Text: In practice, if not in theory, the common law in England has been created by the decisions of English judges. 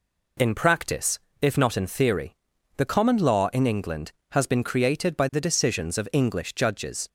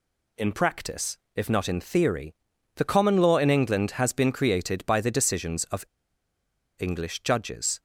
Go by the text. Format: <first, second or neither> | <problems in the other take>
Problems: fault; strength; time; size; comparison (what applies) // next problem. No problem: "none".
first | pauses between "of" and "English"; noticeable; at 5.8 s; 0.96 s long